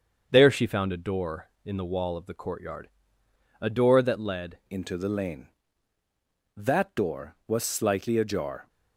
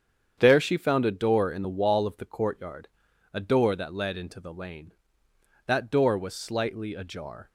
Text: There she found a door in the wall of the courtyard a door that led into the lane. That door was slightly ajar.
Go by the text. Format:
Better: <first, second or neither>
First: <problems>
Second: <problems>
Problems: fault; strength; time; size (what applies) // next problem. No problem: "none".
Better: second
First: starts louder than the rest; until 1.3 s; 7 dB // pauses between "courtyard" and "a"; noticeable; at 2.8 s; 0.72 s long // changes voice at "into"; from 4.7 s on; 3.9 s long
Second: starts louder than the rest; strong; until 1.3 s; 8 dB // pauses between "courtyard" and "a"; noticeable; at 2.8 s; 0.46 s long